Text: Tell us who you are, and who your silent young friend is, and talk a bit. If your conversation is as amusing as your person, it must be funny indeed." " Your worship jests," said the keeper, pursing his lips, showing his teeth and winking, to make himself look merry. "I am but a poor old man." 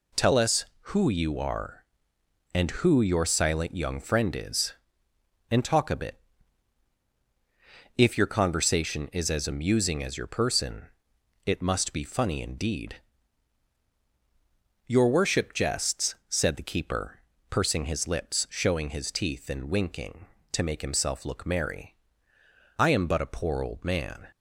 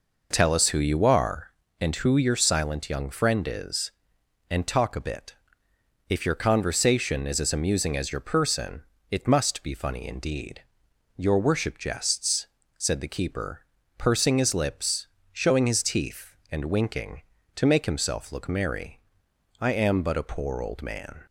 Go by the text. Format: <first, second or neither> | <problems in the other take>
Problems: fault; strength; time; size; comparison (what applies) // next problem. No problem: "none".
first | starts louder than the rest; noticeable; until 1.5 s; 5 dB